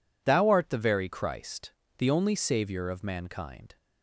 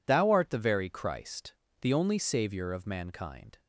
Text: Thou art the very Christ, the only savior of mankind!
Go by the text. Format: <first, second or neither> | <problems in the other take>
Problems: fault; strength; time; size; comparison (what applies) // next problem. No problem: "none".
neither | none